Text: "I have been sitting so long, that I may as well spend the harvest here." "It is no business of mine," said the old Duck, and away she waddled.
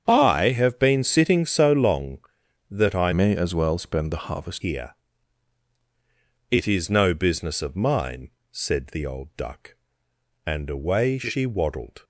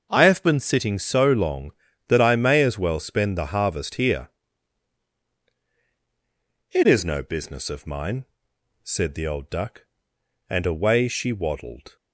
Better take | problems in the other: second | starts louder than the rest; strong; until 1.0 s; 7.5 dB; also in the second // changes voice from "may" to "harvest"; from 3.1 to 4.6 s; 1.5 s long

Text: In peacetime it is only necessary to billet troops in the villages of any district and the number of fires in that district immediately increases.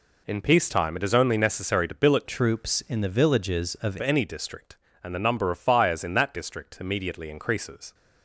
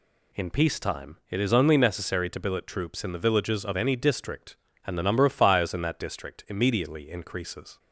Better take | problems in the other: second | changes voice from "troops" to "of"; from 2.2 to 3.9 s; 1.7 s long

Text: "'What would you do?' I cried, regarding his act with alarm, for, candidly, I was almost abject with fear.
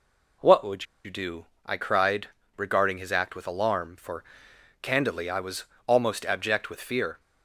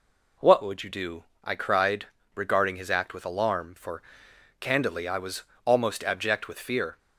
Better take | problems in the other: second | pauses between "would" and "you"; slight; at 0.8 s; 0.20 s long // pauses between "was" and "almost"; slight; at 5.6 s; 0.20 s long; slight in the second

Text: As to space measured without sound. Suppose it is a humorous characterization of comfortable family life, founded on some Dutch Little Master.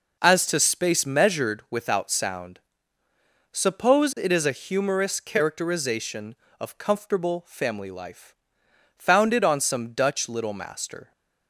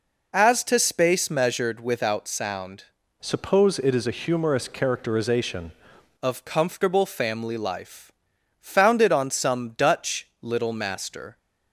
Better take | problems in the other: first | changes voice from "Suppose" to "characterization"; from 3.2 to 5.7 s; 2.5 s long // pauses between "Dutch" and "Little"; slight; at 10.2 s; 0.16 s long

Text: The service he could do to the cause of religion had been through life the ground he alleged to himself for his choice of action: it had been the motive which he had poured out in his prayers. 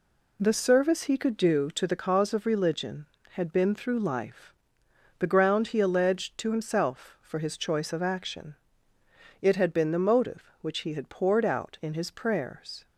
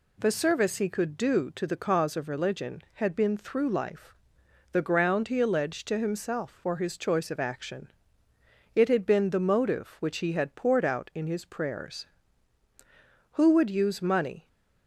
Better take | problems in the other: first | pauses between "life" and "the"; noticeable; at 4.1 s; 0.56 s long; noticeable in the first // goes on to say "Who would use money"; noticeable; from 13.3 s on; 1.1 s long

